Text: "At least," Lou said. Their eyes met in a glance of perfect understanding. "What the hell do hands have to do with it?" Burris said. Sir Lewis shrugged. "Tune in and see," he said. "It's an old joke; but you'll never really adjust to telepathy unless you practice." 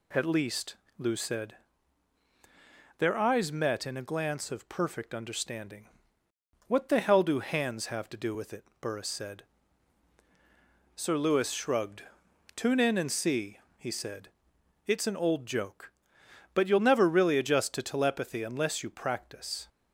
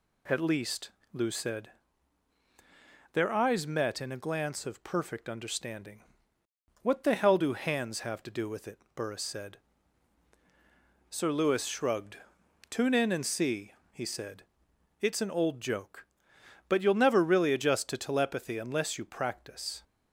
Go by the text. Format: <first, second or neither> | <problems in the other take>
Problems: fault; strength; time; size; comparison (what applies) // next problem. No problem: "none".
neither | none